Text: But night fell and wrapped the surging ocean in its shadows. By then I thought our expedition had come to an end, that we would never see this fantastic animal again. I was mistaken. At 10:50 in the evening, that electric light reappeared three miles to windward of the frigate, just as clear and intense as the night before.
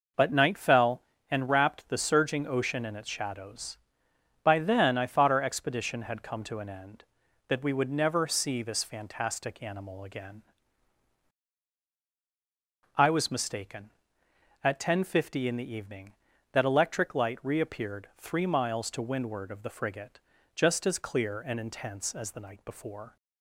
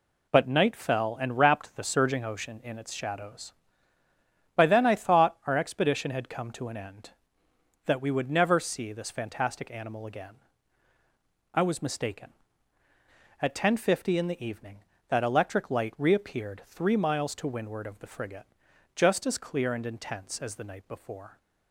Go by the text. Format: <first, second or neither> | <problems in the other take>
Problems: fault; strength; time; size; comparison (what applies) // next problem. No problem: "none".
neither | none